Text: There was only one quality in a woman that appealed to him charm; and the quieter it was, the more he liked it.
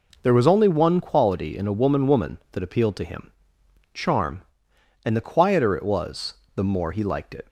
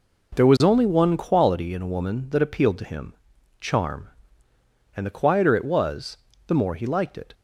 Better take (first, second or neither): second